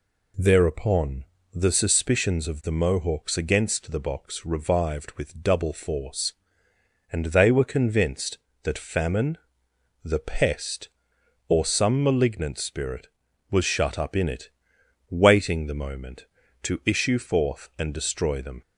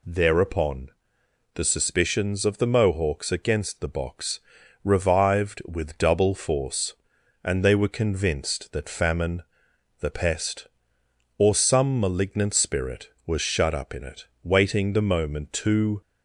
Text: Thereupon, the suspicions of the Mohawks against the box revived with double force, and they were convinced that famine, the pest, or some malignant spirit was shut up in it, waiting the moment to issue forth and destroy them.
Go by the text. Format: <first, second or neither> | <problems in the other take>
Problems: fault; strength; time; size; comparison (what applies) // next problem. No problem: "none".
first | pauses between "box" and "revived"; at 4.3 s; 0.44 s long // stops before "issue forth and destroy them"; at 16.0 s